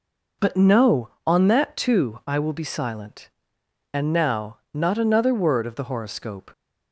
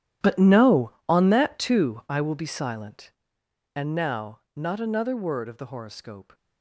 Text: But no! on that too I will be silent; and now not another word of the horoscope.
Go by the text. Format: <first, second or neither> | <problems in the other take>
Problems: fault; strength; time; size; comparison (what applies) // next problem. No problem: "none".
first | gets quieter; strong; throughout; 16.5 dB // pauses between "now" and "not"; slight; at 4.3 s; 0.16 s long; slight in the first